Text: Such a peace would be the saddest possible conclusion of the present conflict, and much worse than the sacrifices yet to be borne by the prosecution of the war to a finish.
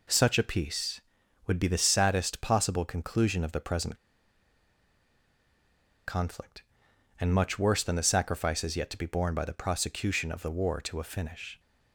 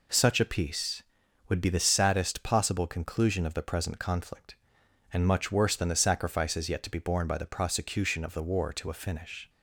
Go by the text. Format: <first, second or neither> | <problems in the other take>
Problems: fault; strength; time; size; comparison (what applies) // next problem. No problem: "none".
second | pauses between "present" and "conflict"; strong; at 3.9 s; 2.1 s long